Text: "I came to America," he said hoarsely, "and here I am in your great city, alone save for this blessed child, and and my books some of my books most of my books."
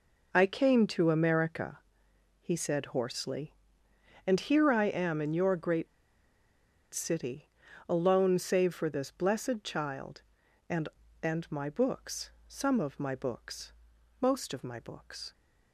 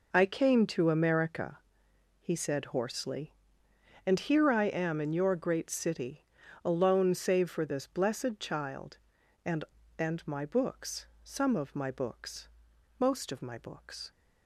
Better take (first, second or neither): second